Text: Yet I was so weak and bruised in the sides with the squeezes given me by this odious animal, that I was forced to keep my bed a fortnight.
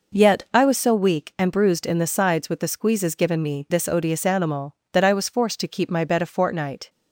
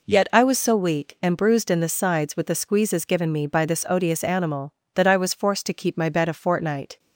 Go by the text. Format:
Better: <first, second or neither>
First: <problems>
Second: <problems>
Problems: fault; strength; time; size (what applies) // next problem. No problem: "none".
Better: second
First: skips "by"; at 3.6 s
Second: none